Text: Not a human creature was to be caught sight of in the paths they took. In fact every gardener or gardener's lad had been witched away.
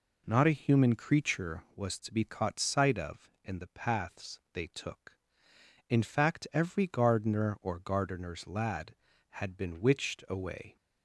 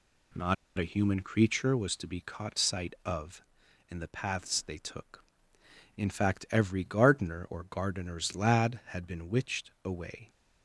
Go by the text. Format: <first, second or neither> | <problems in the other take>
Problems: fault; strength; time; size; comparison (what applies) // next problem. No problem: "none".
first | pauses between "Not" and "a"; slight; at 0.5 s; 0.22 s long